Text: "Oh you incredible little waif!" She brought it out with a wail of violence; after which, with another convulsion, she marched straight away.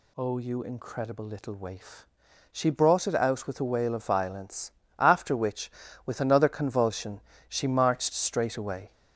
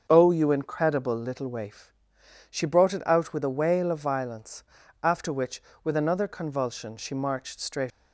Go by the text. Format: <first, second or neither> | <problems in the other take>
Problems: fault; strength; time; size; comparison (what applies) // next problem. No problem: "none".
first | starts louder than the rest; until 1.1 s; 7 dB // stops before "away"; at 7.9 s